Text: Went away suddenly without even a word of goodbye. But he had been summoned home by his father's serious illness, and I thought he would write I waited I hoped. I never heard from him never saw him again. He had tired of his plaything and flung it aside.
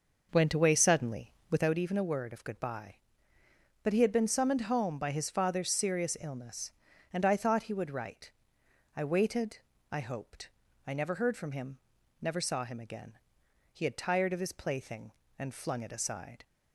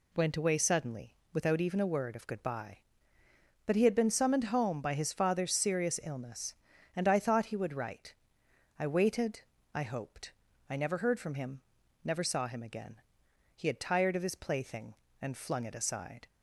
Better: second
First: starts louder than the rest; noticeable; until 1.7 s; 5.5 dB // pauses between "suddenly" and "without"; slight; at 1.3 s; 0.18 s long // pauses between "write" and "I"; noticeable; at 8.3 s; 0.64 s long // pauses between "waited" and "I"; slight; at 9.5 s; 0.32 s long // pauses between "him" and "never"; at 11.7 s; 0.42 s long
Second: pauses between "suddenly" and "without"; slight; at 1.1 s; 0.18 s long // pauses between "write" and "I"; noticeable; at 8.1 s; 0.64 s long // pauses between "waited" and "I"; slight; at 9.4 s; 0.32 s long // pauses between "him" and "never"; at 11.6 s; 0.42 s long

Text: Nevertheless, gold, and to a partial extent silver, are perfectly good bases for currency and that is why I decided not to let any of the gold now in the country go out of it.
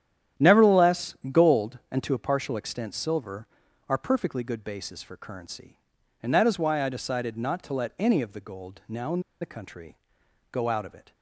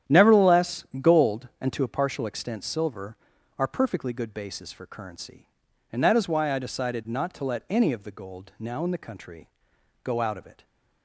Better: second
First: starts louder than the rest; strong; until 1.5 s; 10.5 dB // pauses between "in" and "the"; slight; at 9.1 s; 0.21 s long // pauses between "country" and "go"; noticeable; at 9.9 s; 0.56 s long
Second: starts louder than the rest; strong; until 1.2 s; 10.5 dB // pauses between "country" and "go"; noticeable; at 9.4 s; 0.56 s long

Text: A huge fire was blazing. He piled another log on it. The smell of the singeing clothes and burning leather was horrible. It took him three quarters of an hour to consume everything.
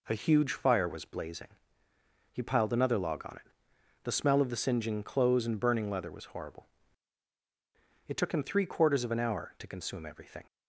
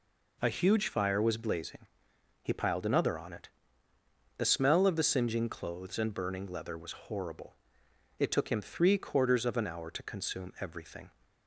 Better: first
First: none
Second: skips "log"; at 3.1 s

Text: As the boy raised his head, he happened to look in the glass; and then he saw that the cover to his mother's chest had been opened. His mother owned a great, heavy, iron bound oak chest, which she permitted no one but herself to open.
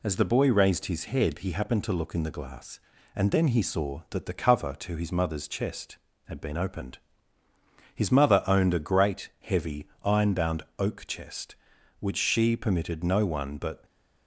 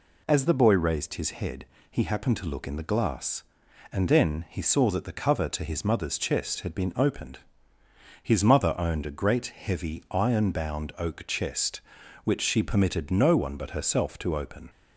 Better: second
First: pauses between "bound" and "oak"; slight; at 10.6 s; 0.16 s long // stops before "herself to open"; at 13.8 s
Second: none

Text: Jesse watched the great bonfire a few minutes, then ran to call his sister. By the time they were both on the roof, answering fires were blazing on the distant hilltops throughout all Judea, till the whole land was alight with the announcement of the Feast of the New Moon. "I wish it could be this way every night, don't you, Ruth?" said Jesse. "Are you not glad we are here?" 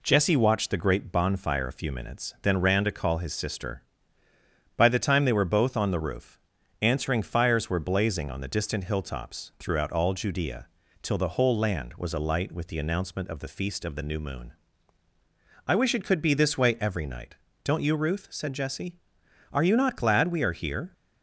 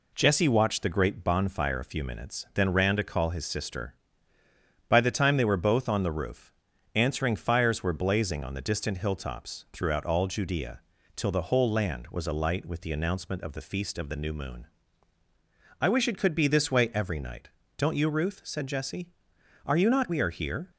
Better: first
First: none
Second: skips "glad"; at 20.0 s

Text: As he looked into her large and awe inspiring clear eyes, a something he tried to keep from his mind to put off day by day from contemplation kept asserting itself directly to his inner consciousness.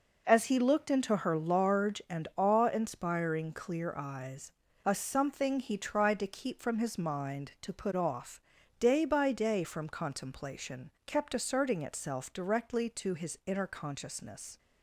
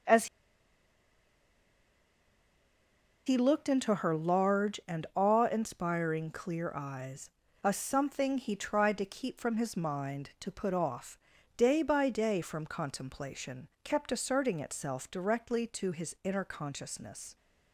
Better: first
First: pauses between "off" and "day"; at 8.3 s; 0.40 s long // pauses between "contemplation" and "kept"; slight; at 10.8 s; 0.16 s long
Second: pauses between "As" and "he"; strong; at 0.2 s; 3.0 s long // pauses between "off" and "day"; at 11.1 s; 0.40 s long // pauses between "contemplation" and "kept"; slight; at 13.6 s; 0.16 s long

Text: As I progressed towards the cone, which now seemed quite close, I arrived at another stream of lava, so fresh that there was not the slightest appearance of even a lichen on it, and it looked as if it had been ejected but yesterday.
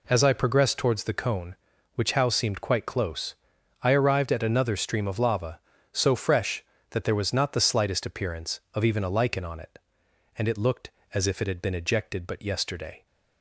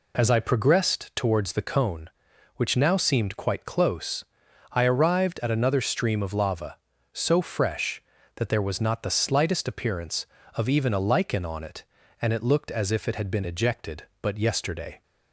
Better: second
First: says "how" for "now"; at 2.1 s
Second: none

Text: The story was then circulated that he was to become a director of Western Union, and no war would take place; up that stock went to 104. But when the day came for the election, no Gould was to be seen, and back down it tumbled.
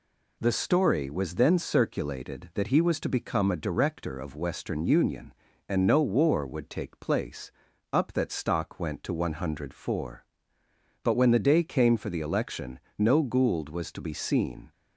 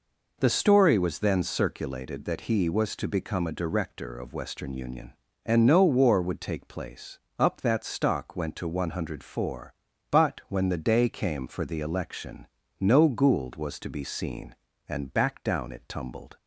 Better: second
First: stops before "and back down it tumbled"; at 14.7 s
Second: none

